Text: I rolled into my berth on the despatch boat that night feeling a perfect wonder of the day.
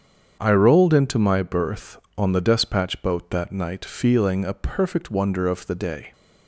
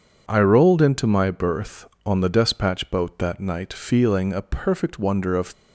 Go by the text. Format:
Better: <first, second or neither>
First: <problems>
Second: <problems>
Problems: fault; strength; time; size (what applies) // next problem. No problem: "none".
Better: first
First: starts louder than the rest; strong; until 1.4 s; 7.5 dB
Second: starts louder than the rest; strong; until 1.2 s; 7 dB // stops before "the day"; at 5.5 s